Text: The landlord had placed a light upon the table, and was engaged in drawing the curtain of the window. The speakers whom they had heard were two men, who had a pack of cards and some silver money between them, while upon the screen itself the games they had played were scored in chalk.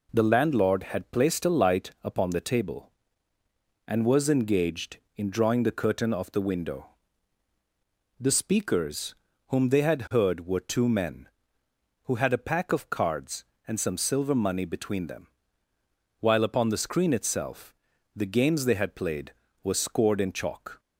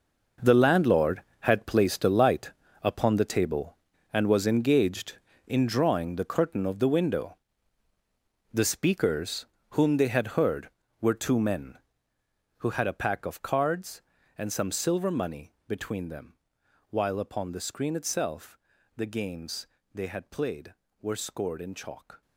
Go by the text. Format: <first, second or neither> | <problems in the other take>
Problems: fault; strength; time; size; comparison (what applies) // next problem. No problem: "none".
first | gets quieter; strong; throughout; 13 dB // pauses between "light" and "upon"; slight; at 2.5 s; 0.30 s long // pauses between "speakers" and "whom"; slight; at 9.4 s; 0.26 s long; slight in the first // pauses between "itself" and "the"; at 18.5 s; 0.38 s long; also in the first // pauses between "games" and "they"; slight; at 19.6 s; 0.26 s long